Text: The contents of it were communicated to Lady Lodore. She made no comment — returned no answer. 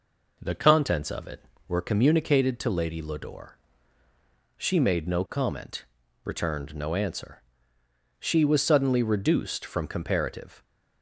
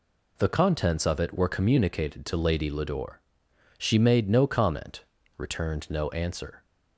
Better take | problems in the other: second | goes on to say "She was suddenly reduced from comparative"; strong; from 8.1 s on; 2.4 s long

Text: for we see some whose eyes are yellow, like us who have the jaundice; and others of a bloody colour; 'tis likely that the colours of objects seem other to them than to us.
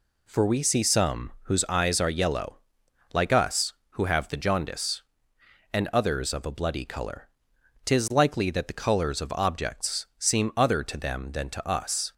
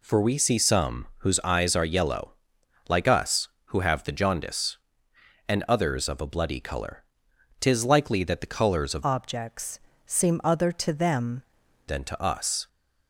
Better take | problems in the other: first | changes voice from "objects" to "them"; from 9.0 to 11.4 s; 2.4 s long // pauses between "objects" and "seem"; slight; at 9.7 s; 0.26 s long

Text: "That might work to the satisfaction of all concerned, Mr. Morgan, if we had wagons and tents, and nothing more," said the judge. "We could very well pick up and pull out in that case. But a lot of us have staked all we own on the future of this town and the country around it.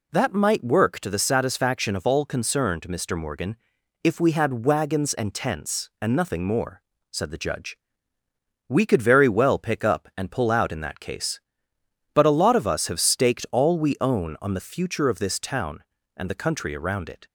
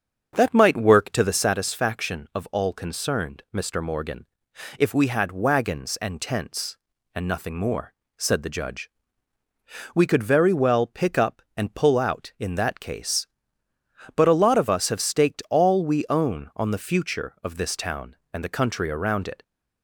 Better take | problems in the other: first | starts louder than the rest; strong; until 1.6 s; 7 dB

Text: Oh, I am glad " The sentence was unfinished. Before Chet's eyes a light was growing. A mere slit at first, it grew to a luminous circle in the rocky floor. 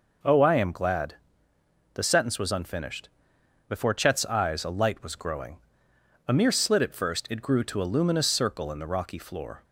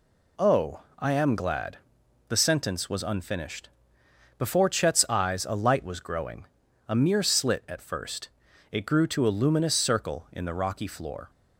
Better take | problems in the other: neither | none

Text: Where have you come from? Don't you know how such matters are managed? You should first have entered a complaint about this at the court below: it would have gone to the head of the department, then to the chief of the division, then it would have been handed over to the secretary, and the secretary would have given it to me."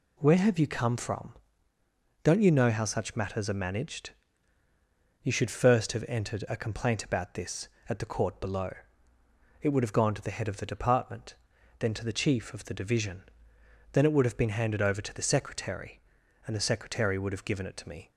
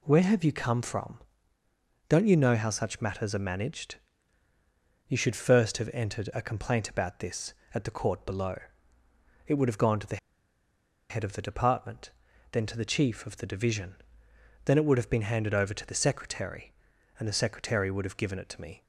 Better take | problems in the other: first | pauses between "the" and "head"; noticeable; at 10.1 s; 0.93 s long

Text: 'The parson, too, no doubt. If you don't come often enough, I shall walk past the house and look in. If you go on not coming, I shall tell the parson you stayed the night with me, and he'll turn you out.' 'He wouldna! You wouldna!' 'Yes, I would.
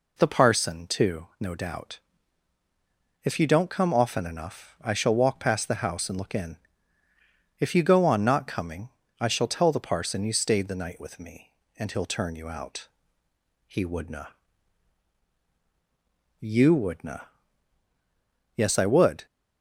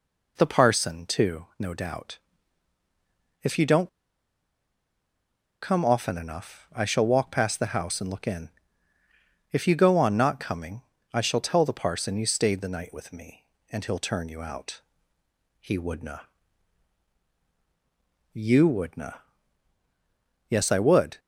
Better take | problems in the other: first | pauses between "don't" and "come"; strong; at 3.8 s; 1.7 s long

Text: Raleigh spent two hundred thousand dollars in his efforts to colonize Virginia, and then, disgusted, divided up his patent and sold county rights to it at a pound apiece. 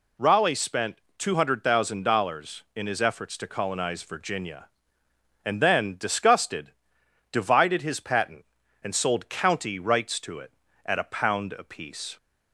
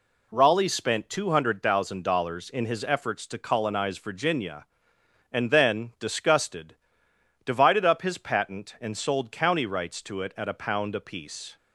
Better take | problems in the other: second | pauses between "spent" and "two"; slight; at 0.9 s; 0.16 s long // skips "up"; at 7.8 s

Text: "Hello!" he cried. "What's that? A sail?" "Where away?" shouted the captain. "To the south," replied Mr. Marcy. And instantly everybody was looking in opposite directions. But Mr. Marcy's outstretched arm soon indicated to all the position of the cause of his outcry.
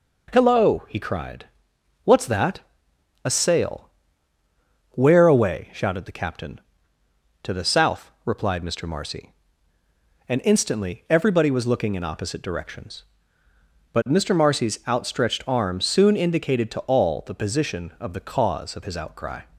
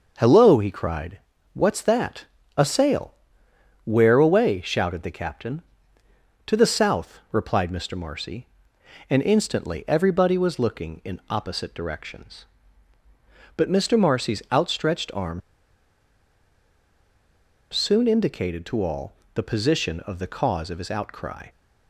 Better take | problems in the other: first | starts louder than the rest; noticeable; until 1.5 s; 6 dB // pauses between "arm" and "soon"; strong; at 15.4 s; 2.3 s long // pauses between "all" and "the"; slight; at 19.1 s; 0.22 s long

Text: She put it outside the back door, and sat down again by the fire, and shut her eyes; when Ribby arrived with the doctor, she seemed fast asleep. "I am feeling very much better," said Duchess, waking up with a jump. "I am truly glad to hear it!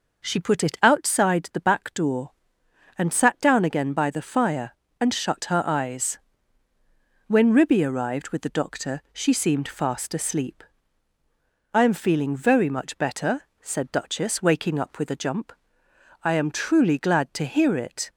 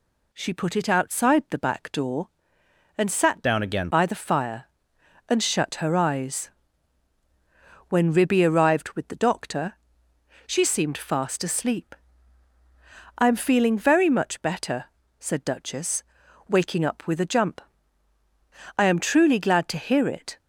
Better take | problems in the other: first | changes voice from "down" to "again"; from 3.4 to 3.8 s; 0.4 s long

